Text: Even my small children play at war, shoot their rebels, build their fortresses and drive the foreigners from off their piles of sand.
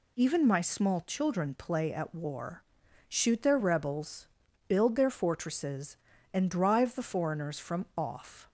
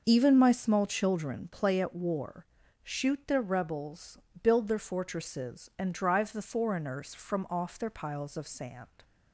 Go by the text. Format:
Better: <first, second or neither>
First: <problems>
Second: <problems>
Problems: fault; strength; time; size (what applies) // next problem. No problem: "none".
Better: second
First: stops before "their piles of sand"; at 8.4 s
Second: none